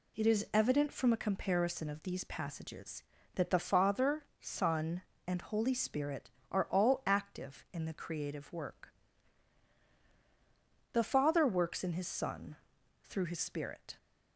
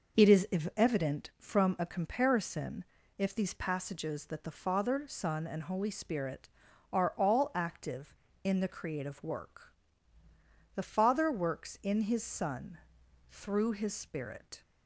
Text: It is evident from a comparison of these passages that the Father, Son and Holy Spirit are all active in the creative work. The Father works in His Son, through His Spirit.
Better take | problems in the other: first | pauses between "is" and "evident"; slight; at 0.4 s; 0.30 s long // says "if" for "of"; at 3.1 s

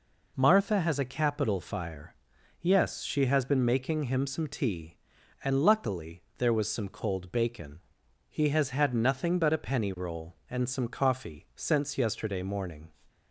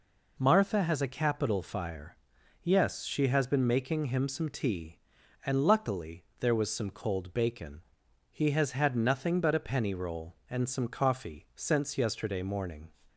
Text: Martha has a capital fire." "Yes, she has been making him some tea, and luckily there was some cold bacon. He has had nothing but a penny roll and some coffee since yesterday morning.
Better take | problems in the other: neither | pauses between "luckily" and "there"; slight; the same in both

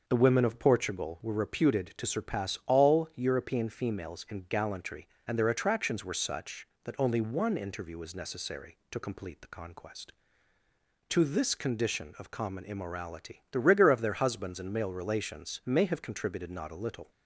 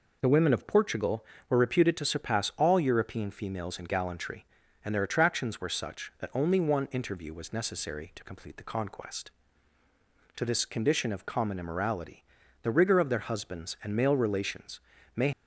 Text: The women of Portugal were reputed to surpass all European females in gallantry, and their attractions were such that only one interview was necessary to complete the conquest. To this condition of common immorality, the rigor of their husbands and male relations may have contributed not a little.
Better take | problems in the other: first | pauses between "relations" and "may"; slight; at 14.8 s; 0.36 s long // stops before "have contributed not a little"; at 15.3 s

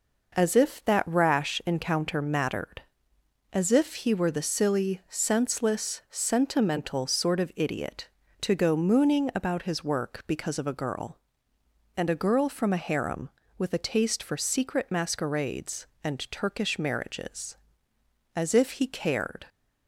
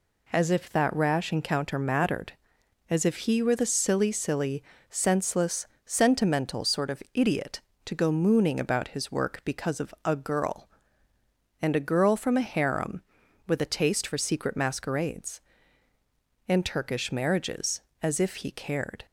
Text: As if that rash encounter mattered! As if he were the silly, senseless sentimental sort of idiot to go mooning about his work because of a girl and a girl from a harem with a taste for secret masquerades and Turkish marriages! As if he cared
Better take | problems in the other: first | says "silly" twice; at 4.1 s // pauses between "senseless" and "sentimental"; slight; at 5.6 s; 0.20 s long

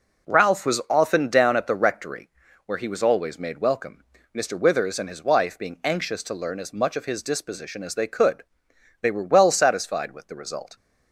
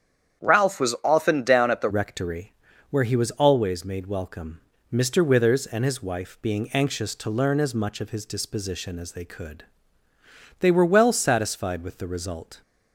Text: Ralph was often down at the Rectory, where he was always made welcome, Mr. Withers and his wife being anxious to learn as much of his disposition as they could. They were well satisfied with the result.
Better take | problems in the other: first | starts louder than the rest; strong; until 1.4 s; 8.5 dB // changes voice at "Rectory"; from 1.8 s on; 10.8 s long

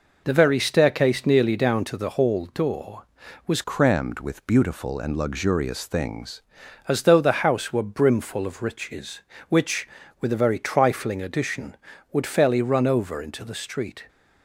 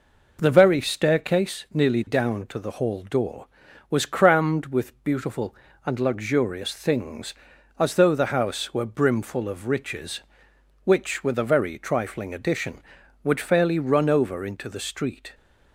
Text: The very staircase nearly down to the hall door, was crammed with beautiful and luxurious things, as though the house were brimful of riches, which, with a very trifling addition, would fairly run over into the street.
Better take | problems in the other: second | changes voice from "crammed" to "things"; from 3.6 to 6.4 s; 2.8 s long

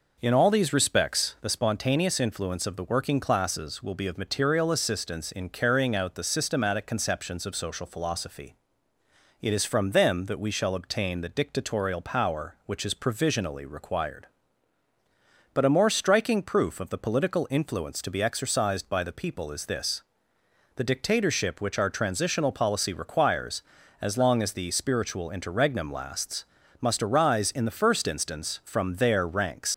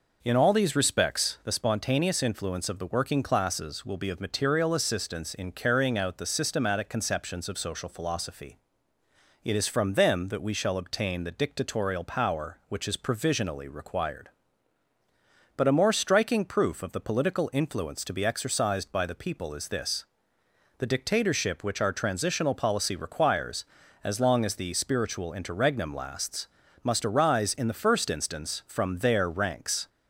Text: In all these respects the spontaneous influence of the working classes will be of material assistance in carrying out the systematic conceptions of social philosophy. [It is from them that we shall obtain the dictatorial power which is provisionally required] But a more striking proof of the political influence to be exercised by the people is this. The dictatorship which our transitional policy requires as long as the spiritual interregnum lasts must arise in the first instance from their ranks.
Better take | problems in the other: second | pauses between "lasts" and "must"; slight; at 26.4 s; 0.36 s long; slight in the second // leaves "ranks" unfinished; at 29.7 s; 115 ms

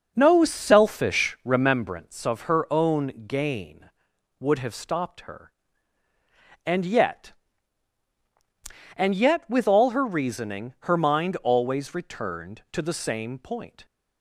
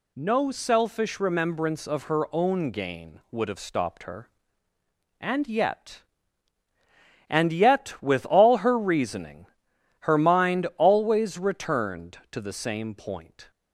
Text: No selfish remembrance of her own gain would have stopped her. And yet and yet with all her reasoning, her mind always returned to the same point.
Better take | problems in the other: second | starts louder than the rest; noticeable; until 1.8 s; 6 dB

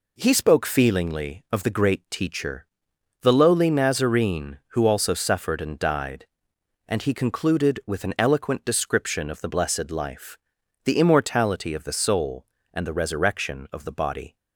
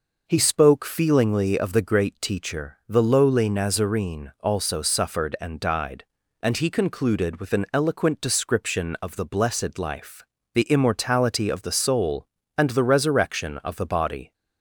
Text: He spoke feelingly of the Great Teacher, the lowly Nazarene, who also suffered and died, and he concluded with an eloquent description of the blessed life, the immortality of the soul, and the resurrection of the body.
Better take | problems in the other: first | skips "who"; at 4.3 s

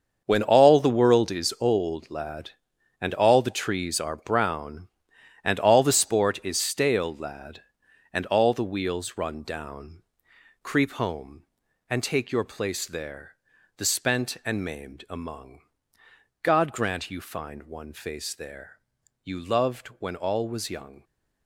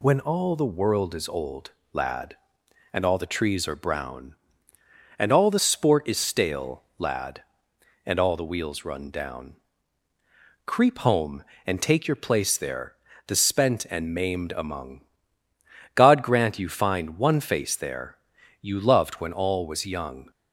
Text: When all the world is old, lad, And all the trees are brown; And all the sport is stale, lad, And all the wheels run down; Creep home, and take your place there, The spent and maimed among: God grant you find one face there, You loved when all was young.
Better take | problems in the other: second | gets quieter; strong; throughout; 11.5 dB

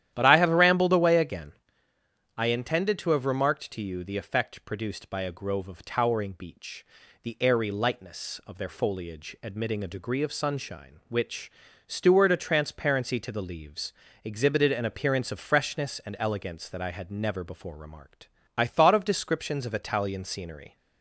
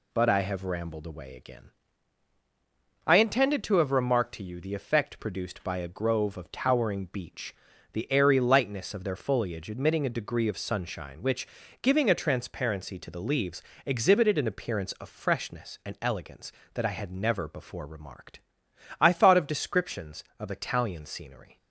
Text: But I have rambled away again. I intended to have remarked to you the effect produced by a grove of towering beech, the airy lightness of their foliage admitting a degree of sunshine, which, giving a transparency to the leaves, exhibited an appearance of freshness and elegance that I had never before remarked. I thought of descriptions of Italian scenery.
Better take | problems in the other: second | starts louder than the rest; strong; until 1.1 s; 11.5 dB // says "steward" for "giving"; at 11.8 s

